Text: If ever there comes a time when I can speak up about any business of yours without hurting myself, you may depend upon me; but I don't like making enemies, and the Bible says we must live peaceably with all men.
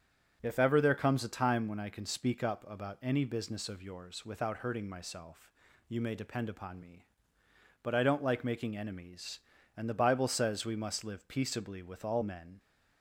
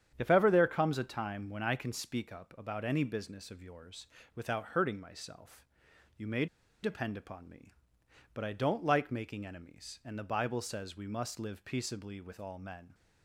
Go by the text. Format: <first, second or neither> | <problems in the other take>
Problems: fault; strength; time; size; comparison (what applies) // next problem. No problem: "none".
first | starts louder than the rest; strong; until 1.1 s; 9 dB; strong in the first // pauses between "yours" and "without"; slight; at 4.0 s; 0.30 s long // pauses between "may" and "depend"; at 6.4 s; 0.37 s long